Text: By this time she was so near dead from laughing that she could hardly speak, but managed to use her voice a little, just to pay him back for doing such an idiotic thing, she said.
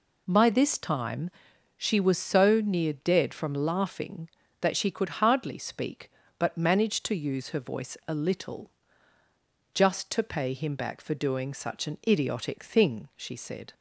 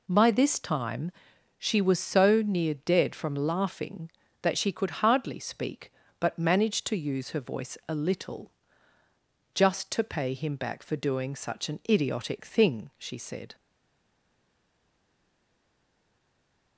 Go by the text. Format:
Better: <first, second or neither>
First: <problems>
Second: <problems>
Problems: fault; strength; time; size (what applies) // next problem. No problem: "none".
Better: first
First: pauses between "time" and "she"; noticeable; at 1.3 s; 0.46 s long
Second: pauses between "time" and "she"; noticeable; at 1.1 s; 0.46 s long // stays silent after the last word; strong; from 13.5 s on; 3.2 s long